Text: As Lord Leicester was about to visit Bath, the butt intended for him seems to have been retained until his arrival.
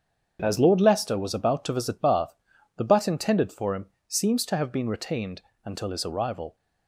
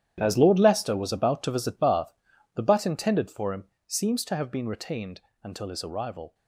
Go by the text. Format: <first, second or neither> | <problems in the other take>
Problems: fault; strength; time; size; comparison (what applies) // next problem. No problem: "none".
first | gets quieter; strong; throughout; 13.5 dB // starts louder than the rest; strong; until 1.2 s; 10.5 dB; strong in the first // pauses between "him" and "seems"; slight; at 3.6 s; 0.20 s long; slight in the first // pauses between "retained" and "until"; slight; at 5.2 s; 0.23 s long; slight in the first